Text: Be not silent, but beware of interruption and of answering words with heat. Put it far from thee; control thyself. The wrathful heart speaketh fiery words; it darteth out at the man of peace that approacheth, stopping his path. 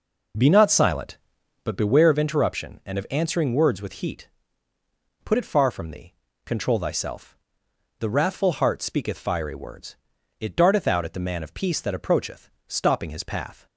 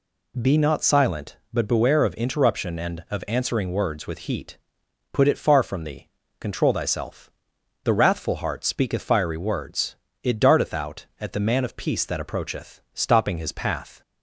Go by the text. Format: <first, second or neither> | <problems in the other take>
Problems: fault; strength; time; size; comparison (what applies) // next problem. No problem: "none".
second | starts louder than the rest; noticeable; until 2.0 s; 4.5 dB